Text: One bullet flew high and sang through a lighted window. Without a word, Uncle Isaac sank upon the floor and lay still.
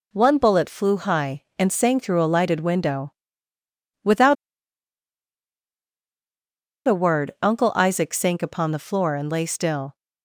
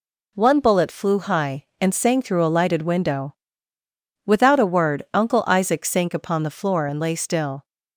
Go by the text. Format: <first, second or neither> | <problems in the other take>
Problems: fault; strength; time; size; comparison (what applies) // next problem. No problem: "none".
second | pauses between "Without" and "a"; strong; at 4.3 s; 2.5 s long